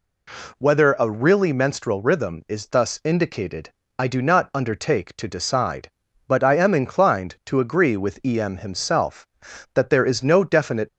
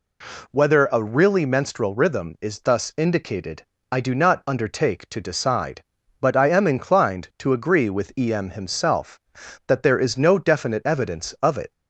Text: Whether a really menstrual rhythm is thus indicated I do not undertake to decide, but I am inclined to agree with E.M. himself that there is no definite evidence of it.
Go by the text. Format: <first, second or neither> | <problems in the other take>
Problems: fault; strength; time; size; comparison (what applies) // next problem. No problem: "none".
second | pauses between "indicated" and "I"; slight; at 3.7 s; 0.26 s long; slight in the second // stops before "evidence of it"; at 10.8 s